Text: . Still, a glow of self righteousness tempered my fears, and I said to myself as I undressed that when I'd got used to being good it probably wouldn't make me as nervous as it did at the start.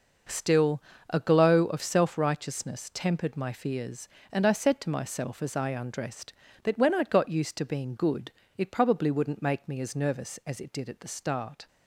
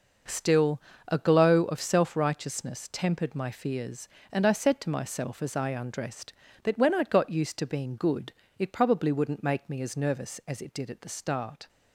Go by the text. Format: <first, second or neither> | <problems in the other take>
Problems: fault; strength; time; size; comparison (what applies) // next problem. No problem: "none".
neither | pauses between "good" and "it"; slight; the same in both